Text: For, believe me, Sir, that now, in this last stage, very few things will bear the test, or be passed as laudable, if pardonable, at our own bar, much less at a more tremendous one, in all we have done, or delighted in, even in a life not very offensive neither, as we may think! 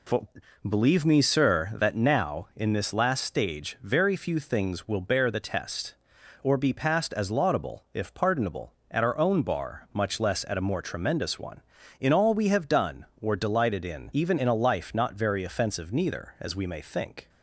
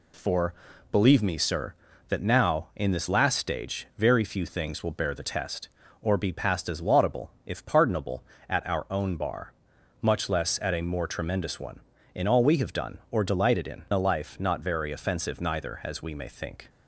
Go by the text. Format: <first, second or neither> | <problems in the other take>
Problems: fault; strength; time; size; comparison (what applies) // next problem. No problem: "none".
first | skips "even in"; at 13.8 s